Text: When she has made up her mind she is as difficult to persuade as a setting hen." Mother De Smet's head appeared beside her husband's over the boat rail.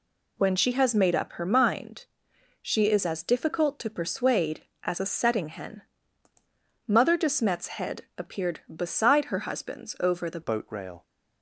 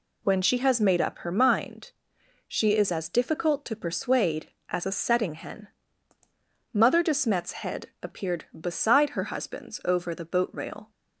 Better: second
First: pauses between "mind" and "she"; noticeable; at 2.0 s; 0.56 s long // changes voice at "boat"; from 10.4 s on; 0.6 s long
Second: pauses between "mind" and "she"; noticeable; at 1.9 s; 0.56 s long

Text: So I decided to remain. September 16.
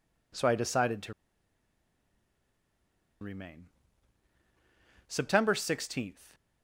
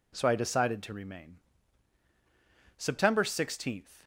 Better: second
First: pauses between "to" and "remain"; strong; at 1.1 s; 2.0 s long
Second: none

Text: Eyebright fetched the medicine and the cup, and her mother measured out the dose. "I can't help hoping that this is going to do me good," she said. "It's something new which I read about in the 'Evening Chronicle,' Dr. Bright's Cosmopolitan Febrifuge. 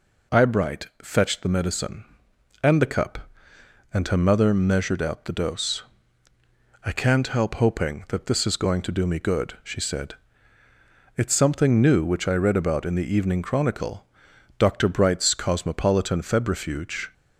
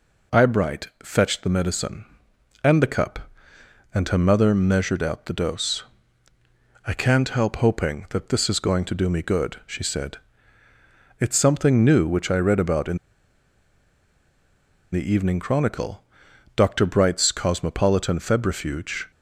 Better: first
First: none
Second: pauses between "in" and "the"; strong; at 12.9 s; 1.9 s long

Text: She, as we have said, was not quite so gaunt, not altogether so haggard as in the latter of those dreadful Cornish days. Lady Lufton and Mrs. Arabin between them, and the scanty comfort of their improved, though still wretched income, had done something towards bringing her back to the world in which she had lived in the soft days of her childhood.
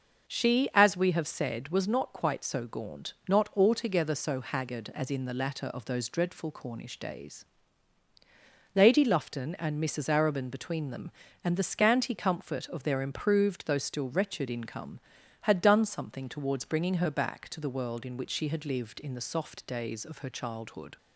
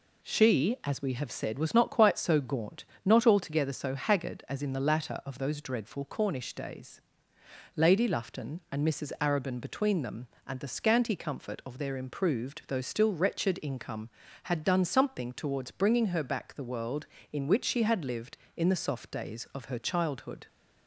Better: first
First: none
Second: skips "to"; at 16.5 s

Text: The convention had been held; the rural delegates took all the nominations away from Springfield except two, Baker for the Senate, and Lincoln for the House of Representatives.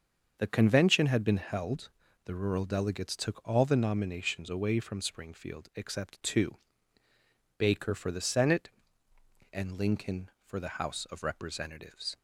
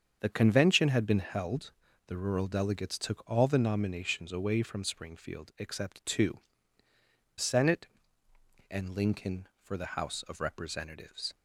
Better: first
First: starts louder than the rest; until 1.4 s; 6.5 dB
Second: starts louder than the rest; strong; until 1.2 s; 7 dB // skips "Baker for the"; at 6.8 s

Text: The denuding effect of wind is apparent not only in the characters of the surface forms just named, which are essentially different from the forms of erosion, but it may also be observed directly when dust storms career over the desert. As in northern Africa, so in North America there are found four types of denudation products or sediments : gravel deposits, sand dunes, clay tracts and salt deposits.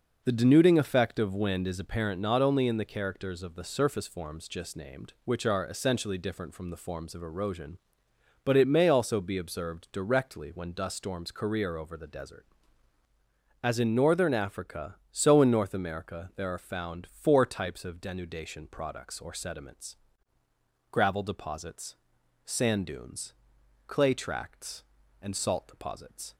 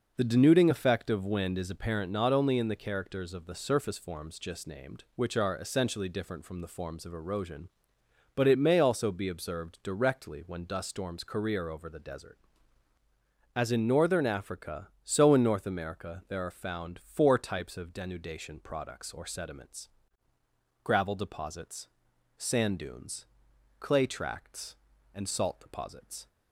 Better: neither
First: none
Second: none

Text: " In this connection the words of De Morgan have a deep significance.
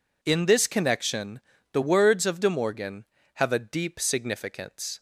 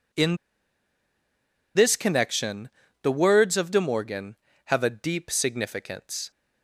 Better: first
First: pauses between "connection" and "the"; slight; at 1.4 s; 0.31 s long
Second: pauses between "In" and "this"; strong; at 0.3 s; 1.3 s long // pauses between "connection" and "the"; slight; at 2.7 s; 0.32 s long

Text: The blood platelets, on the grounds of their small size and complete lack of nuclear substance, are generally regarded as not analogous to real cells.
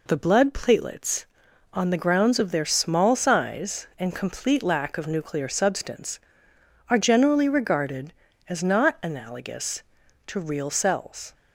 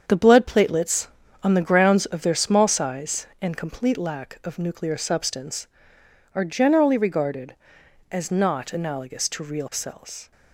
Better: first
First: none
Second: gets quieter; strong; throughout; 8 dB

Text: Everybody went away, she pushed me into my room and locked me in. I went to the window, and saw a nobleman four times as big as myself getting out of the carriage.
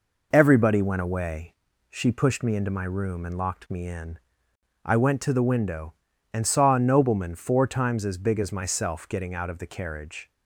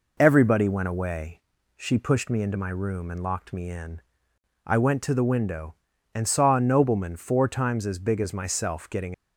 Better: first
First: none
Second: stops before "out of the carriage"; at 9.1 s

